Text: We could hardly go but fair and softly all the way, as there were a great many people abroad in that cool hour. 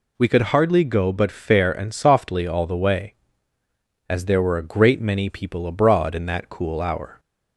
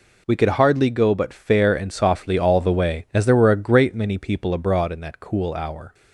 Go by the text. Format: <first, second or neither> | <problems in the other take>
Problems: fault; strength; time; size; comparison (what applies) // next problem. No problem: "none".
neither | none